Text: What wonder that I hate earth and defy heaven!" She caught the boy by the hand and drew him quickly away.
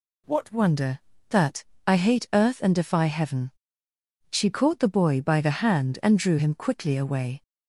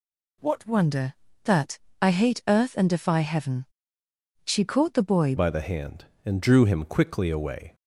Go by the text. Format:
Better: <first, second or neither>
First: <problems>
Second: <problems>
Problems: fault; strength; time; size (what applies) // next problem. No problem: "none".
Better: first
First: pauses between "that" and "I"; slight; at 1.6 s; 0.24 s long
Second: pauses between "that" and "I"; slight; at 1.7 s; 0.24 s long // changes voice at "by"; from 5.3 s on; 2.4 s long